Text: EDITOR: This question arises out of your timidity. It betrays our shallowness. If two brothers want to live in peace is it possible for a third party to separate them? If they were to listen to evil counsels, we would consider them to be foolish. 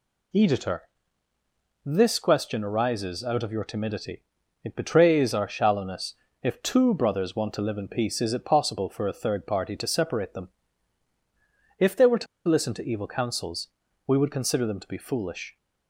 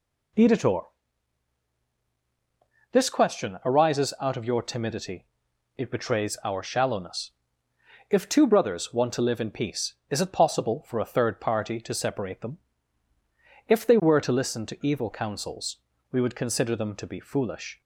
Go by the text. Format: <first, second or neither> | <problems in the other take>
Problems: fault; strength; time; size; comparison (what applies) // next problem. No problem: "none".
second | pauses between "to" and "listen"; slight; at 12.2 s; 0.22 s long